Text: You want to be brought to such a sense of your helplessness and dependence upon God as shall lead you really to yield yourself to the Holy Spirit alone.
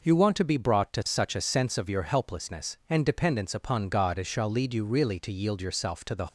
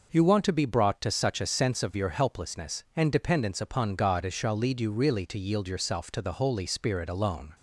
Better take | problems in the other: second | stops before "Holy Spirit alone"; at 6.2 s

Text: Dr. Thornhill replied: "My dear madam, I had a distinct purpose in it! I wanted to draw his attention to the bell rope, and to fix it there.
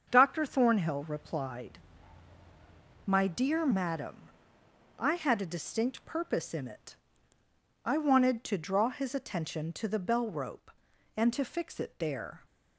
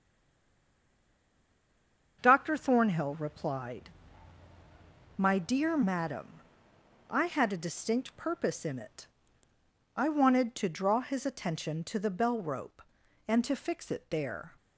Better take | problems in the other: first | stays silent before the first word; until 2.2 s; 2.2 s long // starts louder than the rest; until 3.2 s; 7 dB; also in the first

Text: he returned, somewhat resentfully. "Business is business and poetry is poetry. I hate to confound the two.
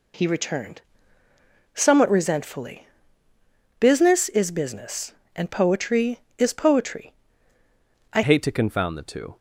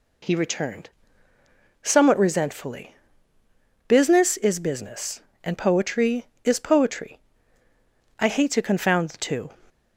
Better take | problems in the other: second | changes voice at "hate"; from 8.2 s on; 1.1 s long

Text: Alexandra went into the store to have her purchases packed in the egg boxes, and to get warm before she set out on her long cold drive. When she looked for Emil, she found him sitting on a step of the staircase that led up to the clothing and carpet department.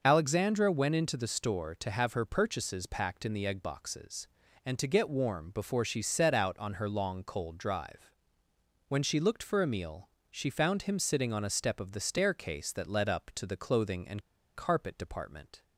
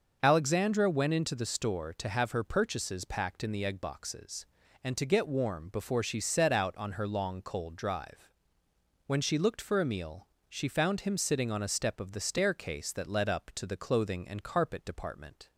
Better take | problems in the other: second | starts louder than the rest; until 1.0 s; 6.5 dB; also in the second // pauses between "and" and "carpet"; slight; at 14.2 s; 0.33 s long

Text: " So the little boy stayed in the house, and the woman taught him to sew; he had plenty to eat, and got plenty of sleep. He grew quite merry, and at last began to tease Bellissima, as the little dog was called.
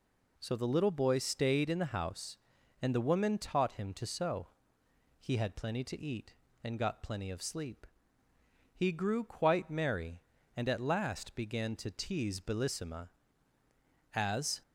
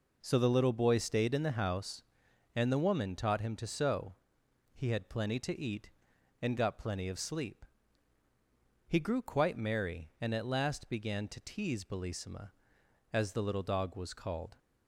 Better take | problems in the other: second | stops before "the little dog was called"; at 14.6 s

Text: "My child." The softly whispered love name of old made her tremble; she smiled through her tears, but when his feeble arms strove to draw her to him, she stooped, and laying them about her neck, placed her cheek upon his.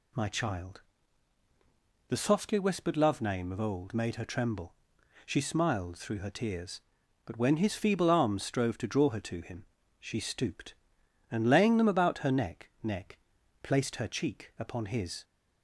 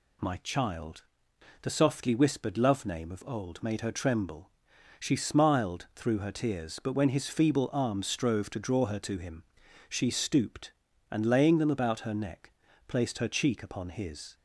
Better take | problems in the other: second | says "neck" twice; at 12.8 s

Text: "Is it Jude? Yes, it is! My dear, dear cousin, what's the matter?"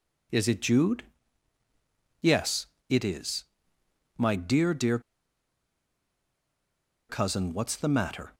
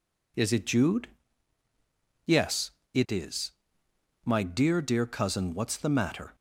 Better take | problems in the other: second | pauses between "dear" and "cousin"; strong; at 4.9 s; 2.0 s long

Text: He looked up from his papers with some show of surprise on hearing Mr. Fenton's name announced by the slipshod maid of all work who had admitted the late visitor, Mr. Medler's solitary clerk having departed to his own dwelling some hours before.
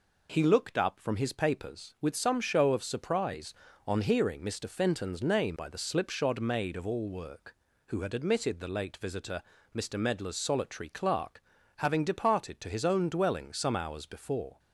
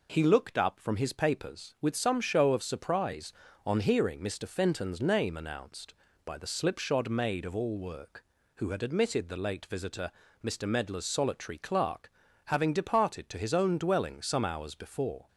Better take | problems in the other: second | skips "announced"; at 5.5 s // pauses between "clerk" and "having"; slight; at 11.4 s; 0.36 s long; slight in the second

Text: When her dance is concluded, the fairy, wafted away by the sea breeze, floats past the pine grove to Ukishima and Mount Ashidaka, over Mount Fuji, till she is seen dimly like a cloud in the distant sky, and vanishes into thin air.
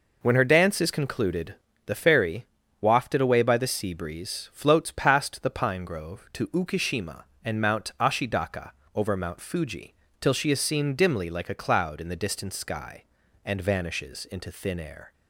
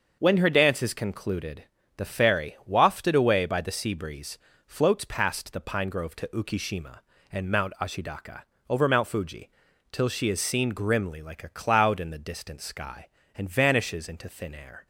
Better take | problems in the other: first | starts louder than the rest; until 1.2 s; 6.5 dB // says "grimly" for "dimly"; at 10.7 s

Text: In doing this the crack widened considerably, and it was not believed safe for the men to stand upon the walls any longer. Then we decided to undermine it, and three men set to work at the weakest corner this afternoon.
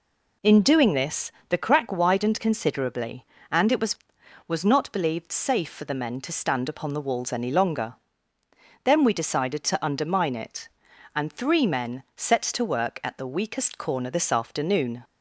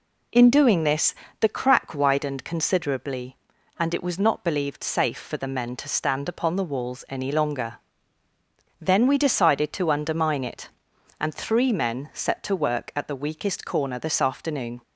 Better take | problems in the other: second | pauses between "this" and "the"; slight; at 1.3 s; 0.16 s long; slight in the second // says "was" twice; at 4.4 s

